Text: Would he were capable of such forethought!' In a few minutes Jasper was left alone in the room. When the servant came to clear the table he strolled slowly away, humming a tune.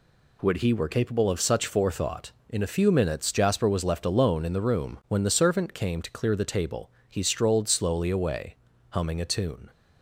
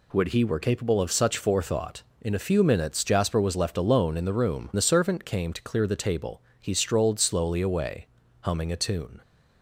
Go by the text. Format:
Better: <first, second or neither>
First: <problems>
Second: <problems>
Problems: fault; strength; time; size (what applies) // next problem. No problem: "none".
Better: first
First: pauses between "table" and "he"; slight; at 6.8 s; 0.20 s long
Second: skips "When"; at 4.7 s // pauses between "table" and "he"; slight; at 6.3 s; 0.20 s long